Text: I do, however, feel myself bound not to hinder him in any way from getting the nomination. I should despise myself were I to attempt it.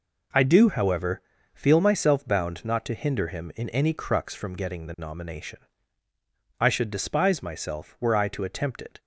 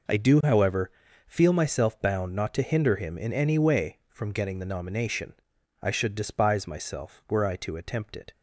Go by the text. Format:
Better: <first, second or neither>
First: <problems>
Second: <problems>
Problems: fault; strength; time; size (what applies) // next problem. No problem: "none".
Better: second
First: says "crux" for "way"; at 3.9 s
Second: none